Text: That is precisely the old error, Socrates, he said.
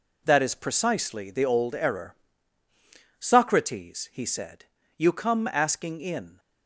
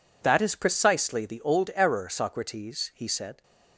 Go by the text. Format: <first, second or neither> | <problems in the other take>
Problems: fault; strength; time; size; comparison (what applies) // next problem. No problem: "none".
second | goes on to say "You come asking in"; from 4.9 s on; 1.4 s long